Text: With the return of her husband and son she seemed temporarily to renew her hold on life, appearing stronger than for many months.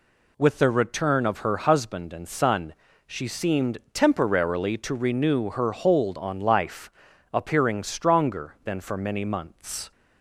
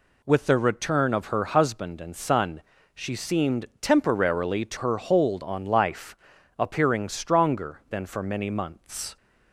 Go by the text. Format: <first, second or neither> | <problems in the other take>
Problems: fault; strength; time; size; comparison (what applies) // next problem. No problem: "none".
first | pauses between "son" and "she"; slight; at 2.6 s; 0.32 s long; slight in the first // skips "renew"; at 4.7 s